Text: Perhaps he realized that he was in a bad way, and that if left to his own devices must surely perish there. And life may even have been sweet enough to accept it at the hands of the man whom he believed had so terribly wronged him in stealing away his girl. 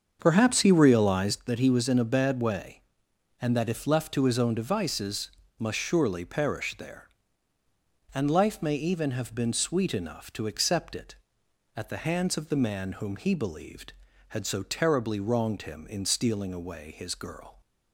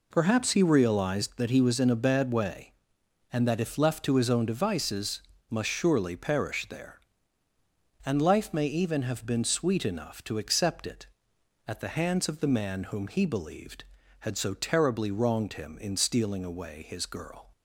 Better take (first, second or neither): second